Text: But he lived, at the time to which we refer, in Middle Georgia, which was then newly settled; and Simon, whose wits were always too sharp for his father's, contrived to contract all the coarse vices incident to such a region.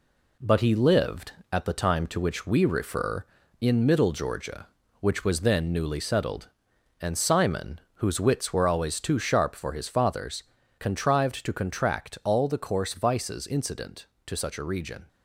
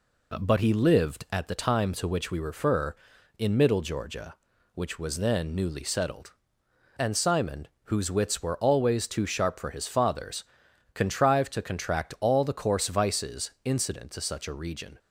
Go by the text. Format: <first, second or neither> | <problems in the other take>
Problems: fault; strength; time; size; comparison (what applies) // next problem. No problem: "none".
second | gets quieter; noticeable; throughout; 4.5 dB